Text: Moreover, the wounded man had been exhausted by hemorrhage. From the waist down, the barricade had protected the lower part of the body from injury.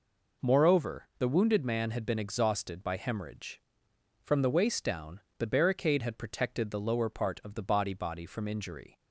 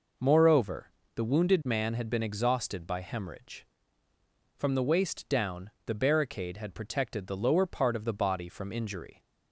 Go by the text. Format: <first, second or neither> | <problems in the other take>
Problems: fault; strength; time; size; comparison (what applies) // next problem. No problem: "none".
second | says "body" twice; at 7.9 s